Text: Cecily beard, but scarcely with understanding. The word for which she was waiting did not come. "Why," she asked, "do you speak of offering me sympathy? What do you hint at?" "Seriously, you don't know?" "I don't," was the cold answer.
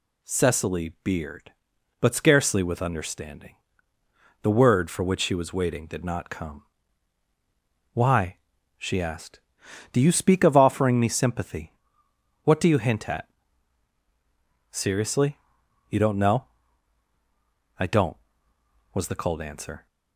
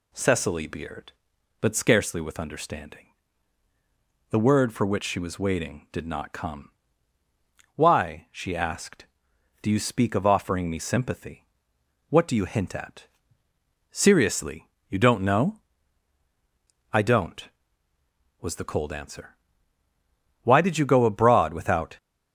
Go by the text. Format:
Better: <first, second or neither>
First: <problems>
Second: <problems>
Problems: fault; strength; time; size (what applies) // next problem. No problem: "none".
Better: first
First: none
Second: goes on to say "Why did you go abroad without"; from 20.4 s on; 1.5 s long